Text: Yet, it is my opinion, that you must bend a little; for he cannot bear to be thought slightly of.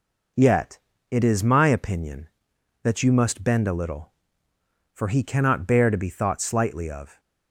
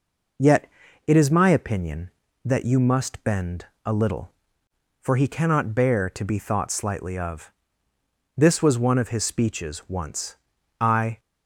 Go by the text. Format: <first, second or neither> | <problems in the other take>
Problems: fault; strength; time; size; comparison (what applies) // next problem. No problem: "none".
first | pauses between "bend" and "a"; slight; at 3.6 s; 0.20 s long // goes on to say "This was one of his speeches once I"; strong; from 8.3 s on; 2.8 s long